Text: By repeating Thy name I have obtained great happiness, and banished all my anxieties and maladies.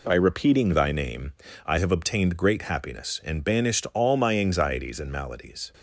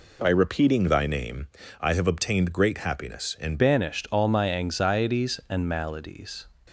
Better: first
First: pauses between "name" and "I"; slight; at 1.3 s; 0.34 s long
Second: pauses between "name" and "I"; slight; at 1.4 s; 0.34 s long // changes voice at "banished"; from 3.5 s on; 2.9 s long

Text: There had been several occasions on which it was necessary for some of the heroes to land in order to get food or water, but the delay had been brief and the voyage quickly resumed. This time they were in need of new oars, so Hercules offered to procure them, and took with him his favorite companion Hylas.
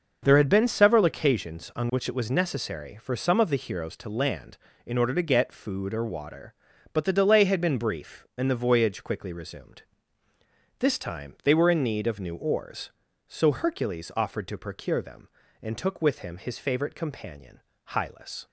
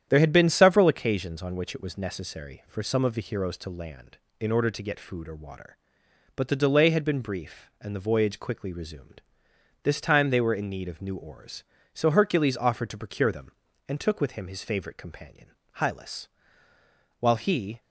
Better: first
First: starts louder than the rest; noticeable; until 1.2 s; 6 dB // pauses between "companion" and "Hylas"; slight; at 17.5 s; 0.30 s long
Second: starts louder than the rest; strong; until 1.0 s; 9.5 dB // pauses between "companion" and "Hylas"; slight; at 15.4 s; 0.28 s long // goes on to say "While he"; from 17.2 s on; 0.60 s long

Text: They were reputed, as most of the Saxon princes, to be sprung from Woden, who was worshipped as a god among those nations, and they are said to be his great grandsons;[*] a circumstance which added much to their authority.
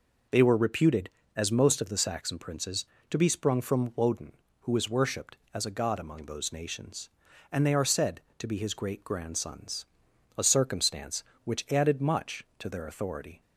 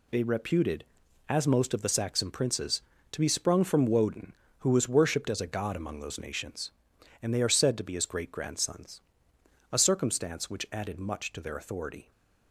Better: first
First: none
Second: skips "were"; at 0.2 s

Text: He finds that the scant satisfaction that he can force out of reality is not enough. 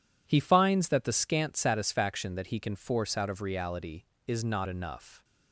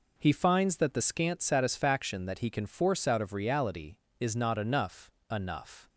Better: first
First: none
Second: says "enough" twice; at 5.3 s

